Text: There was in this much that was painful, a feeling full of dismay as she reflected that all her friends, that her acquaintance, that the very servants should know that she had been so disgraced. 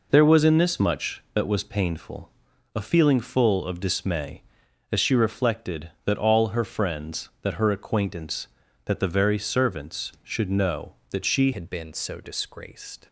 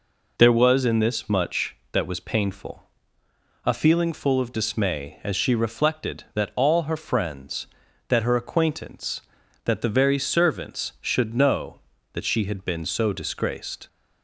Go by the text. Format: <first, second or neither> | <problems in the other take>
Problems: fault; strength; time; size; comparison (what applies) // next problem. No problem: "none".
second | changes voice at "had"; from 11.5 s on; 1.5 s long